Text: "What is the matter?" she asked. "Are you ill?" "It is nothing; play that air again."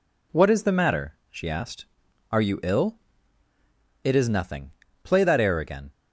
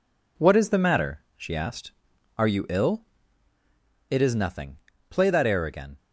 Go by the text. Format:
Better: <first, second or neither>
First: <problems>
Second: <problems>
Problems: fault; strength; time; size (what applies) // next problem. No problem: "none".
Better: first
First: none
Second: gets quieter; noticeable; throughout; 5 dB